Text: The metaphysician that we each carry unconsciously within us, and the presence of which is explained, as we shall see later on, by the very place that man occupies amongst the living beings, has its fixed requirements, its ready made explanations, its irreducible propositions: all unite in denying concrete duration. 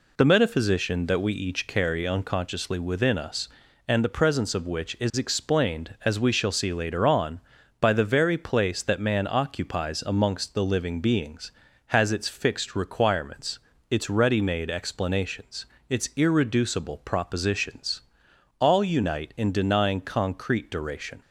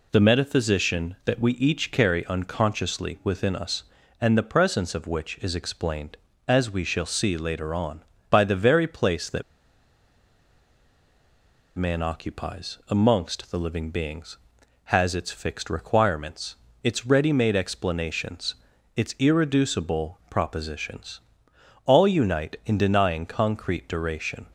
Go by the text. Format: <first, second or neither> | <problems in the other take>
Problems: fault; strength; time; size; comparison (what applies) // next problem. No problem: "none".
first | pauses between "that" and "man"; strong; at 9.4 s; 2.3 s long